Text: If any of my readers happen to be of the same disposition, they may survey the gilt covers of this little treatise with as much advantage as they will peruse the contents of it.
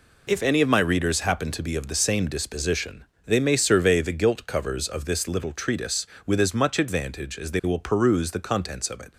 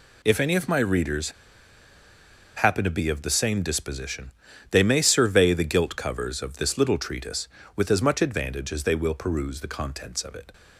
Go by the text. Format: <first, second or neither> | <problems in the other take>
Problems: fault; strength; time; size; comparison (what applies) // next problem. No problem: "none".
first | pauses between "readers" and "happen"; strong; at 1.2 s; 1.2 s long